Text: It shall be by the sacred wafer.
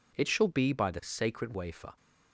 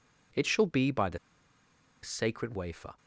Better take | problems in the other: first | pauses between "the" and "sacred"; noticeable; at 1.1 s; 0.84 s long

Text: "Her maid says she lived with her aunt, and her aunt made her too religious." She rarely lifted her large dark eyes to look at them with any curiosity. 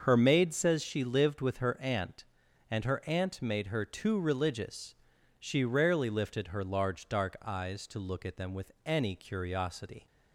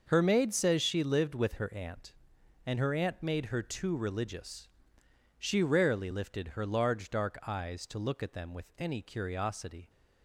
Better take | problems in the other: neither | starts louder than the rest; the same in both

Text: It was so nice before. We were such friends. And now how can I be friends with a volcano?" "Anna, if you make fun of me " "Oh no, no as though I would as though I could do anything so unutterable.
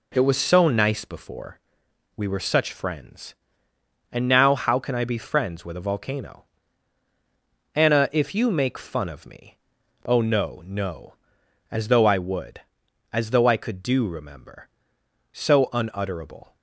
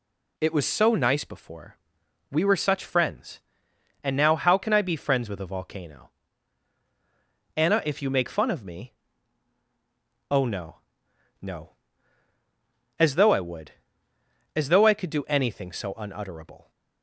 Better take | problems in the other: second | says "remember" for "anything"; at 14.0 s

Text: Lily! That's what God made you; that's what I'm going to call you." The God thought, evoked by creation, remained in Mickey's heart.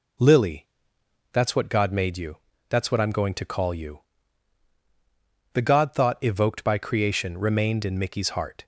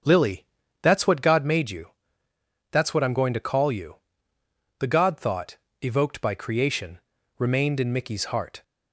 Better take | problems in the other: first | starts louder than the rest; strong; until 1.5 s; 8 dB

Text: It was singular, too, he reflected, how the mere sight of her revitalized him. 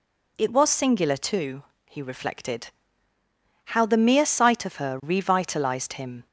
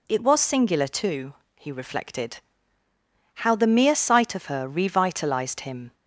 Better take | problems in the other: neither | none

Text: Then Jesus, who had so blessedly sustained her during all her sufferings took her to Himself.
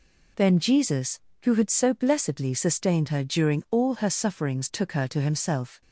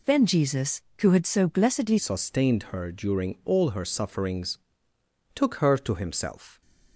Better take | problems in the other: first | changes voice at "sustained"; from 1.9 s on; 4.7 s long // pauses between "sufferings" and "took"; noticeable; at 4.5 s; 0.78 s long

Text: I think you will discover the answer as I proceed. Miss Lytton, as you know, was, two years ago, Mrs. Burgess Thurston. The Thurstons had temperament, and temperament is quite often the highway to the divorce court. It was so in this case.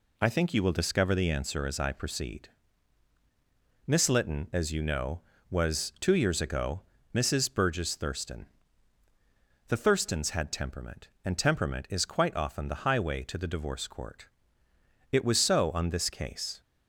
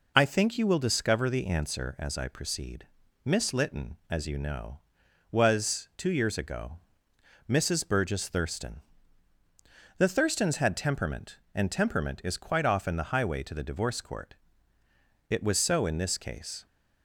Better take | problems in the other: second | says "on" for "in"; at 15.7 s

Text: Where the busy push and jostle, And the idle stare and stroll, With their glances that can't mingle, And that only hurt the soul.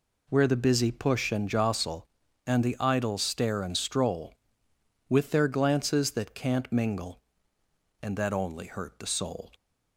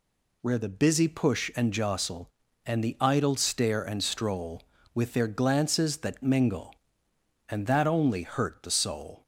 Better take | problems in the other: first | skips "can't"; at 6.2 s

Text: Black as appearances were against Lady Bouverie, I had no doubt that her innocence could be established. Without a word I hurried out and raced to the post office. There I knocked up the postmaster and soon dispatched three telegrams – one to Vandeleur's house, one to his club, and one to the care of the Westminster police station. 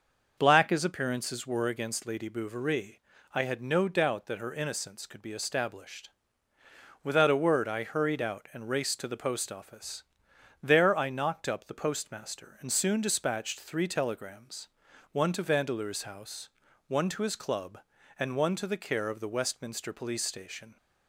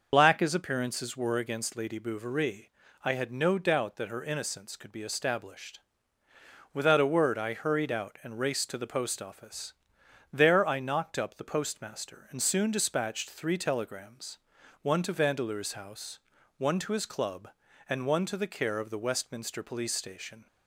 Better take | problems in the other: first | loses the start of "Black"; at 0.1 s; 45 ms // starts louder than the rest; until 1.1 s; 6 dB; noticeable in the first

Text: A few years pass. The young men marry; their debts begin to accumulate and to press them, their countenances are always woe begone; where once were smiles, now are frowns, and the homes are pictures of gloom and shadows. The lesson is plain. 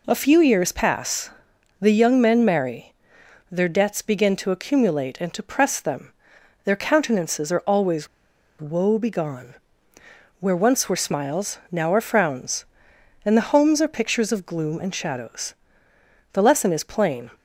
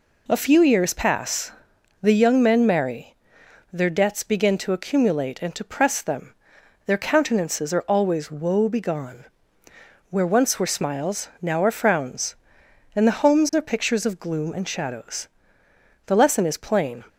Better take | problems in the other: second | pauses between "always" and "woe"; noticeable; at 8.0 s; 0.54 s long

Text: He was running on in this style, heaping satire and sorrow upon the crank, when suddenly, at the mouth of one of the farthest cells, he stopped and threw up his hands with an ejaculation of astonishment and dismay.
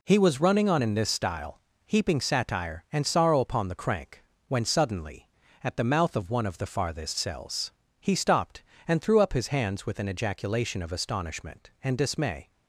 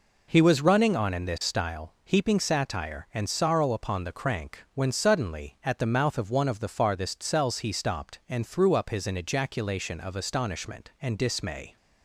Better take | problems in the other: first | skips "hands with"; at 9.0 s

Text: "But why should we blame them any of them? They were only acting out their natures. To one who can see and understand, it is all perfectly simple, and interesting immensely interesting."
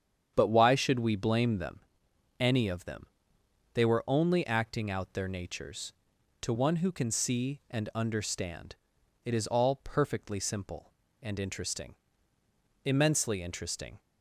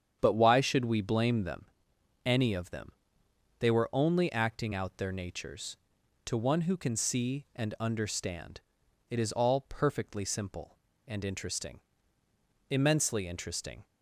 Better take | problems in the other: neither | starts louder than the rest; strong; the same in both // pauses between "them" and "any"; noticeable; the same in both // pauses between "interesting" and "immensely"; noticeable; the same in both

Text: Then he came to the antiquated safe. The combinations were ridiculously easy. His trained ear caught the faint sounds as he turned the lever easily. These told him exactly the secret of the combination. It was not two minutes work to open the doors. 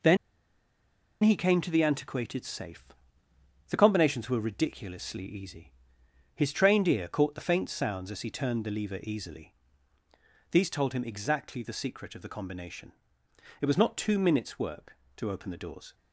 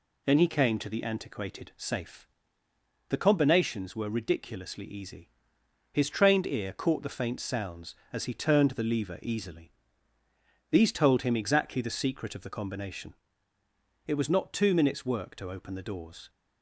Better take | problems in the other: second | pauses between "Then" and "he"; at 0.1 s; 1.0 s long

